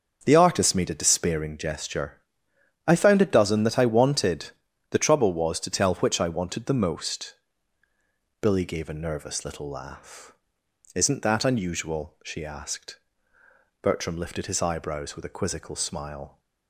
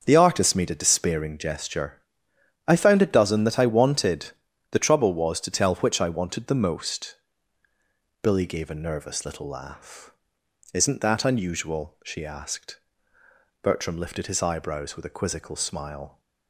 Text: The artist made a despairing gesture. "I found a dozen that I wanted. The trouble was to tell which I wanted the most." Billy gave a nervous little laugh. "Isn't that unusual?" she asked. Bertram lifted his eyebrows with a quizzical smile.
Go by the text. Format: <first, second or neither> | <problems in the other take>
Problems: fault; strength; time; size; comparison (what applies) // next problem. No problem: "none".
neither | starts louder than the rest; the same in both